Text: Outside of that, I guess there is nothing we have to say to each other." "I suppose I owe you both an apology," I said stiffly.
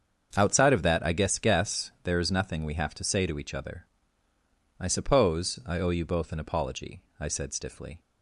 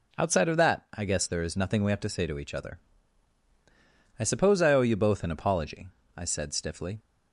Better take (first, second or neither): second